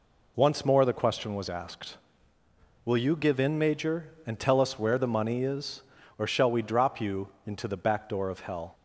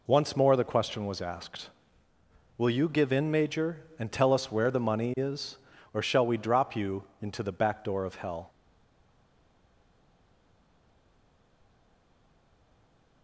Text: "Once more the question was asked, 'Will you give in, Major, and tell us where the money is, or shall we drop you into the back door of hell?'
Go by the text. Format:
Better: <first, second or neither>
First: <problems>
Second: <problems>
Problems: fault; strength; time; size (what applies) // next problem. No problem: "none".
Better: first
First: pauses between "you" and "into"; slight; at 7.2 s; 0.18 s long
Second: pauses between "you" and "into"; slight; at 7.0 s; 0.18 s long // stays silent after the last word; strong; from 8.4 s on; 4.8 s long